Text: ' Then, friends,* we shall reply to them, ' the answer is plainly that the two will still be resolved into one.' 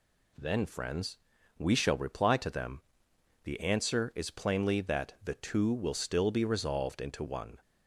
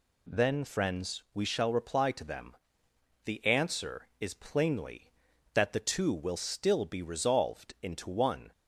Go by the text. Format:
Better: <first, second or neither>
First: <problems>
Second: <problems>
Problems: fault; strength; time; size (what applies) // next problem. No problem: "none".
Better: neither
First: none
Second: none